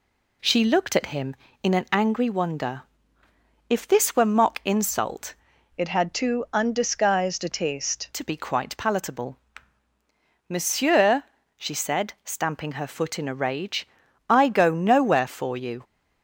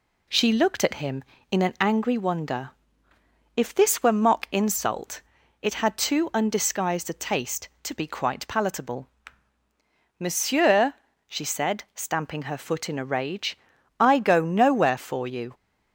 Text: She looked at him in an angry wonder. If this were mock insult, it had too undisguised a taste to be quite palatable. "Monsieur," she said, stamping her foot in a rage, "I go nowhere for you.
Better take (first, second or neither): second